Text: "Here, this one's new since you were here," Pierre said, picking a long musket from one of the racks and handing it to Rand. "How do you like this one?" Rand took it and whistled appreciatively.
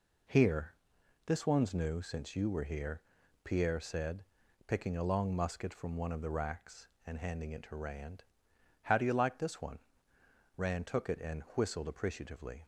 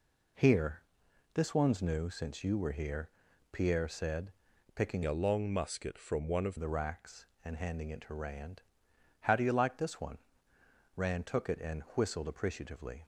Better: first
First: none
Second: changes voice from "a" to "of"; from 5.0 to 6.5 s; 1.5 s long

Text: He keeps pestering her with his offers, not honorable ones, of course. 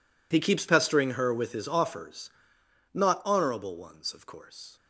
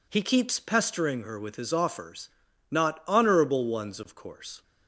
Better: neither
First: none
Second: none

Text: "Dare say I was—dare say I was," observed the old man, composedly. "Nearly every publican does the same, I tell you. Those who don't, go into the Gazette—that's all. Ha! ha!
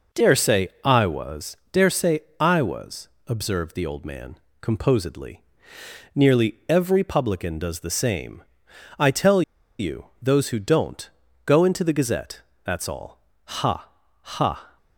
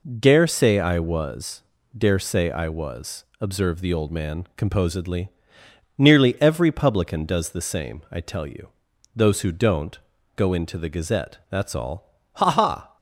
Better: second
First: pauses between "say" and "I"; slight; at 0.6 s; 0.16 s long // pauses between "say" and "I"; slight; at 2.1 s; 0.18 s long // pauses between "tell" and "you"; at 9.4 s; 0.37 s long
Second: none

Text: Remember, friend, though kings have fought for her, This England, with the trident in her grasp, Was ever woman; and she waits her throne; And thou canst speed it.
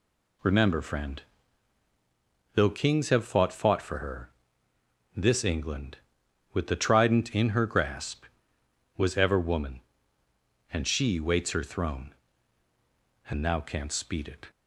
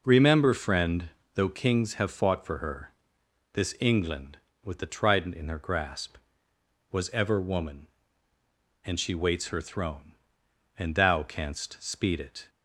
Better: second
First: says "fought" twice; at 3.5 s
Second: none

